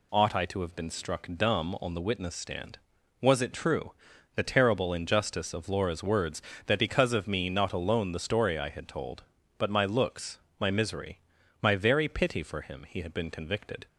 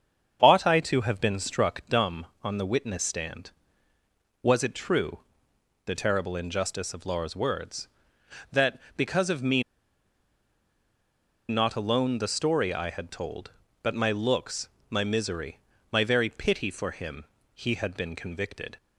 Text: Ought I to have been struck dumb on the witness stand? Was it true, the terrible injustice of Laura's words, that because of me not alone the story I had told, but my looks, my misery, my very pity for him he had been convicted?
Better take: first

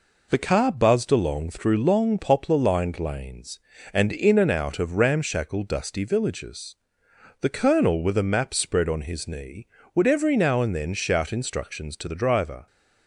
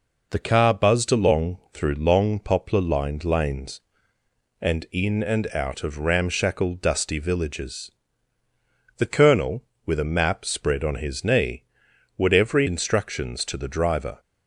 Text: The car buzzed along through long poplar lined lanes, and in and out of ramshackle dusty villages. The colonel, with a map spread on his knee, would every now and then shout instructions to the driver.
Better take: first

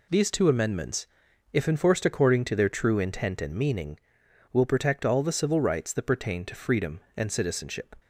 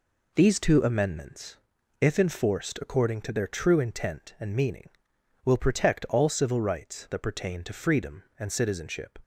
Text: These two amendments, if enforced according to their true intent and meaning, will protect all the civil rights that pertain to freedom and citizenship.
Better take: first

